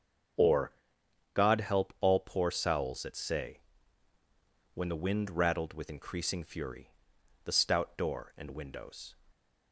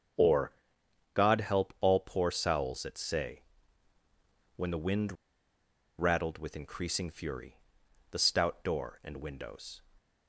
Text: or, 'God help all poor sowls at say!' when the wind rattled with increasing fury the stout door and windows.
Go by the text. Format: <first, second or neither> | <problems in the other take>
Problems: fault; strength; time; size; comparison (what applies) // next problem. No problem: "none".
first | starts louder than the rest; until 1.8 s; 7 dB; also in the first // pauses between "wind" and "rattled"; noticeable; at 5.1 s; 0.85 s long // pauses between "fury" and "the"; noticeable; at 7.5 s; 0.54 s long; noticeable in the first